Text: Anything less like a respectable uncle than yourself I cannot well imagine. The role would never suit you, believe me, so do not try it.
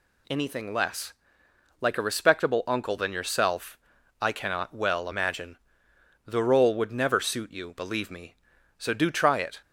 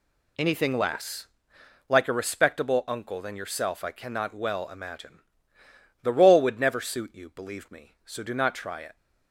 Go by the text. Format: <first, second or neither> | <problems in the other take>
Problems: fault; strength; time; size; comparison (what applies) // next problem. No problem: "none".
second | pauses between "less" and "like"; noticeable; at 1.1 s; 0.70 s long; noticeable in the second // pauses between "yourself" and "I"; at 3.7 s; 0.44 s long // skips "not"; at 9.1 s